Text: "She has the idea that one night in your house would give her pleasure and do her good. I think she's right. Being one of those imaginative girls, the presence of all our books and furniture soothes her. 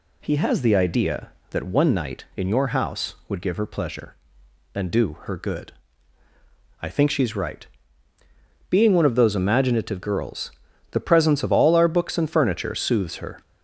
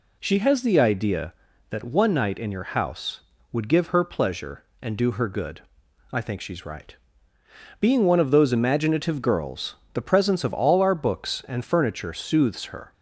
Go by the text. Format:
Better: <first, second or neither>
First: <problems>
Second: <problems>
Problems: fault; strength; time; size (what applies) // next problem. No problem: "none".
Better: second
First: says "He" for "She"; at 0.2 s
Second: none